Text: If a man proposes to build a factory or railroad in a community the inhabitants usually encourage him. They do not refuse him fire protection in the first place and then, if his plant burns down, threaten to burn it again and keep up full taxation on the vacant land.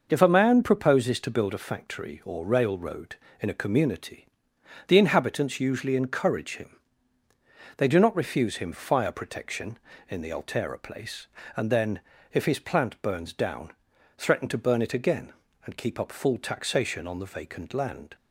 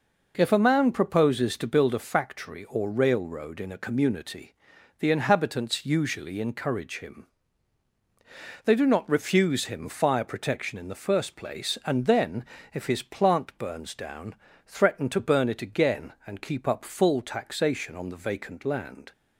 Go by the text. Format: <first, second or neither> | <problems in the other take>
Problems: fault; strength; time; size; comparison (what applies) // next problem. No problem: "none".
second | pauses between "community" and "the"; noticeable; at 4.2 s; 0.62 s long; noticeable in the second // says "altera" for "first"; at 10.3 s